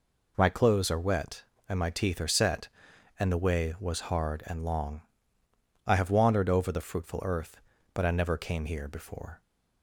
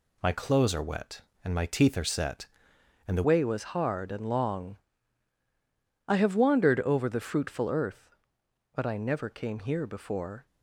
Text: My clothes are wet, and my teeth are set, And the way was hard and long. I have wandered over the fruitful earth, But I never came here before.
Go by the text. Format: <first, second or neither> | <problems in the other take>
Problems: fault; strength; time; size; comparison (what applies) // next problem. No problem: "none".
first | changes voice at "way"; from 3.2 s on; 7.2 s long